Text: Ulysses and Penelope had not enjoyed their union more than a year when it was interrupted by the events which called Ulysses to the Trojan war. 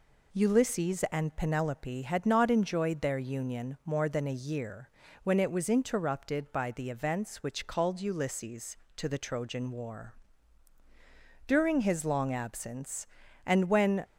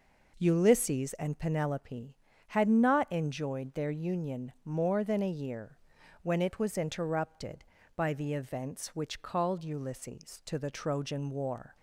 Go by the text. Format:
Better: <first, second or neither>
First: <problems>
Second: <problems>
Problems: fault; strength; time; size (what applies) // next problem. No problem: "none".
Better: second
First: pauses between "year" and "when"; slight; at 4.8 s; 0.36 s long // goes on to say "During his long absence and when"; strong; from 11.4 s on; 2.5 s long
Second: pauses between "year" and "when"; at 5.7 s; 0.44 s long